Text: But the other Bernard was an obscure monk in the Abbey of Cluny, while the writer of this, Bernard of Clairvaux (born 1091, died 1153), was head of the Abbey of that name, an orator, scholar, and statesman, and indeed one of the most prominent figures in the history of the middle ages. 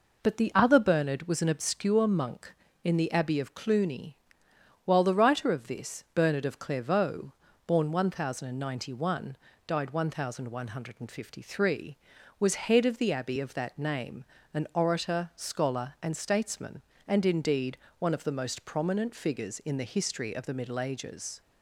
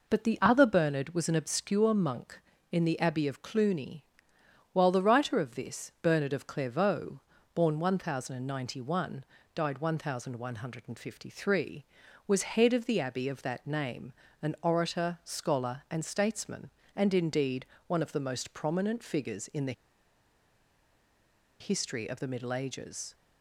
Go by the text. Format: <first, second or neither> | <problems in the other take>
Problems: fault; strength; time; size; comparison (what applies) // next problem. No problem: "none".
first | pauses between "indeed" and "one"; slight; at 17.6 s; 0.22 s long; slight in the first // pauses between "the" and "history"; strong; at 19.7 s; 1.8 s long